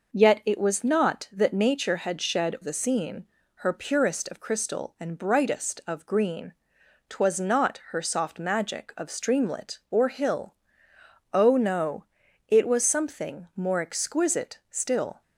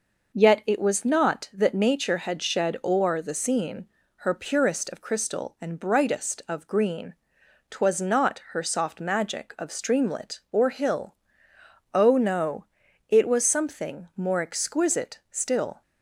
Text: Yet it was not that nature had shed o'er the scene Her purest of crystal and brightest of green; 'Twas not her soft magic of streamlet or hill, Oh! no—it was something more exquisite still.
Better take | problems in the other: second | skips "o'er"; at 2.5 s // pauses between "scene" and "Her"; slight; at 3.2 s; 0.30 s long; slight in the second

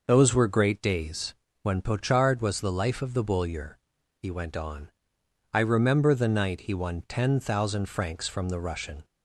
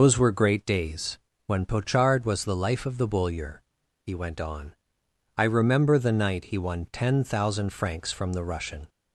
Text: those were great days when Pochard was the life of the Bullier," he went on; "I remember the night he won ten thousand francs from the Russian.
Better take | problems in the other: first | loses the start of "those"; at 0.0 s; 95 ms // pauses between "days" and "when"; slight; at 1.1 s; 0.30 s long; slight in the first

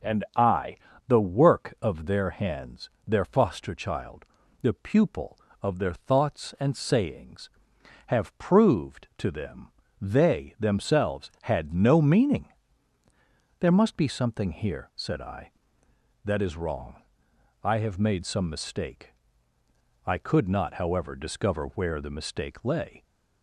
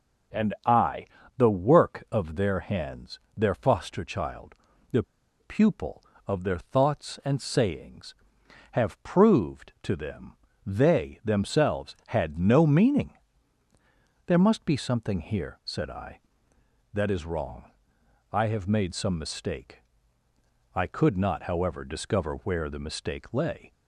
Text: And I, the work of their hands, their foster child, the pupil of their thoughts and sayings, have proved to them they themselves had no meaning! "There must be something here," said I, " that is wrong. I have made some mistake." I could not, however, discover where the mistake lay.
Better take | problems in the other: first | pauses between "the" and "pupil"; at 5.0 s; 0.37 s long // pauses between "them" and "they"; slight; at 10.3 s; 0.32 s long; slight in the first

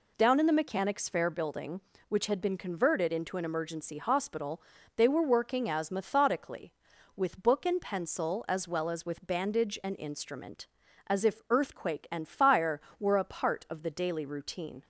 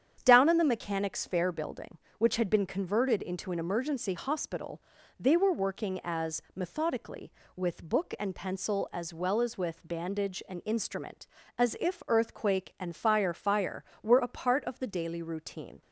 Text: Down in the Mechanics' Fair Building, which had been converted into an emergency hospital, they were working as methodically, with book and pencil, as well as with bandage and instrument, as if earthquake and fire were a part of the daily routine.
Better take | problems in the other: first | starts louder than the rest; strong; until 1.2 s; 9 dB // says "fire" twice; at 13.3 s

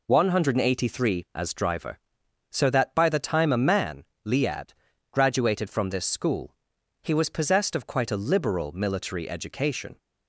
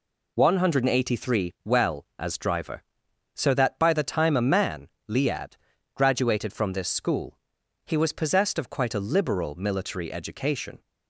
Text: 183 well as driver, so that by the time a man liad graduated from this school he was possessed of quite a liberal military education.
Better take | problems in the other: second | skips "well"; at 1.2 s // pauses between "man" and "liad"; slight; at 4.0 s; 0.22 s long; slight in the second // pauses between "liad" and "graduated"; at 4.7 s; 0.40 s long; also in the second // pauses between "school" and "he"; noticeable; at 6.5 s; 0.48 s long; noticeable in the second

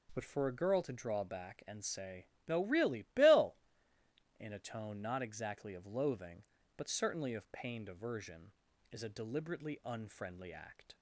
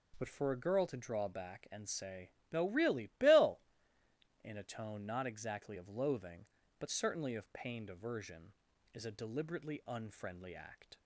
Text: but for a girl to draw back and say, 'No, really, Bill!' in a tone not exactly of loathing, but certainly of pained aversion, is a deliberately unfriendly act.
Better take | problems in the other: neither | none

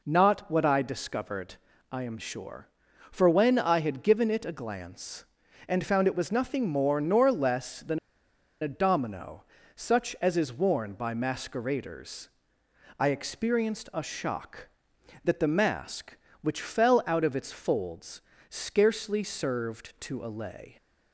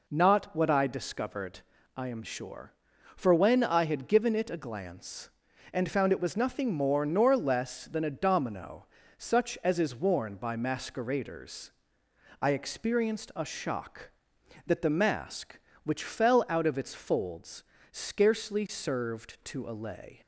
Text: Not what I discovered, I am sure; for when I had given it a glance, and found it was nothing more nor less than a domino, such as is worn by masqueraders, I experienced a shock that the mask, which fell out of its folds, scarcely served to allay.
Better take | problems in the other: second | pauses between "than" and "a"; noticeable; at 7.9 s; 0.63 s long

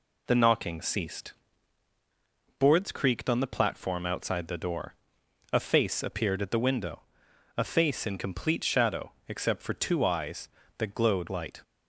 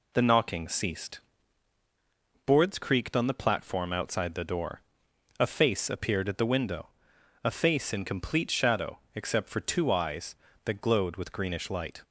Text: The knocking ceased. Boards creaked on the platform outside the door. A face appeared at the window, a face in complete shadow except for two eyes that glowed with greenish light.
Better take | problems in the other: second | pauses between "shadow" and "except"; slight; at 9.1 s; 0.16 s long; slight in the second // skips "with greenish"; at 11.2 s

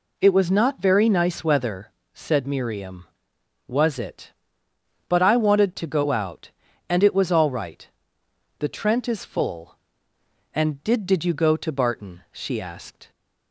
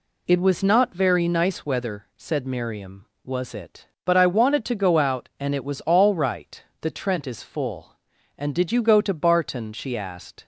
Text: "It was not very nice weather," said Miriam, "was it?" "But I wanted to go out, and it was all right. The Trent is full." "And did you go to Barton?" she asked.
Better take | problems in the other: second | says "did" twice; at 11.0 s

